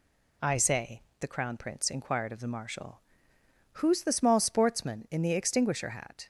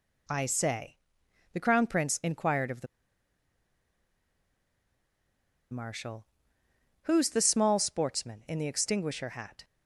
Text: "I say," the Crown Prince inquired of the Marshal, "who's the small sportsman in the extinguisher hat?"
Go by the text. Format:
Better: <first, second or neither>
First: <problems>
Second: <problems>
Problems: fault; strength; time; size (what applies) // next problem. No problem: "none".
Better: first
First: none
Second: pauses between "the" and "Marshal"; strong; at 2.8 s; 2.8 s long